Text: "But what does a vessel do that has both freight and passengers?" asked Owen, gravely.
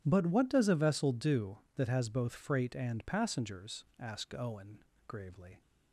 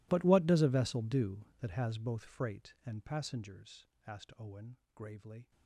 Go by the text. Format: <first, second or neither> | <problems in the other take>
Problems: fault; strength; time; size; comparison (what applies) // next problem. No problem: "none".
first | gets quieter; strong; throughout; 24.5 dB